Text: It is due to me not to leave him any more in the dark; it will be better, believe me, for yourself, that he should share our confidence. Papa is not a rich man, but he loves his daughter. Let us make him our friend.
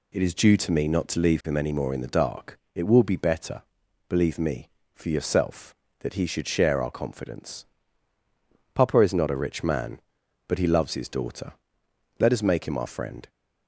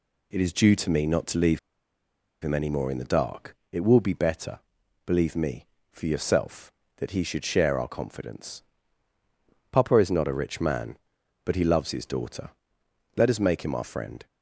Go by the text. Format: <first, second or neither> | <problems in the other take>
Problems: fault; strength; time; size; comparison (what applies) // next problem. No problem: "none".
first | pauses between "leave" and "him"; noticeable; at 1.5 s; 0.82 s long